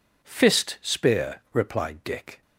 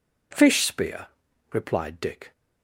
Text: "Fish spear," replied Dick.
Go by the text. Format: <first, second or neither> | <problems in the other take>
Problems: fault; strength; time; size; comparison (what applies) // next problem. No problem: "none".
second | says "Fist" for "Fish"; at 0.2 s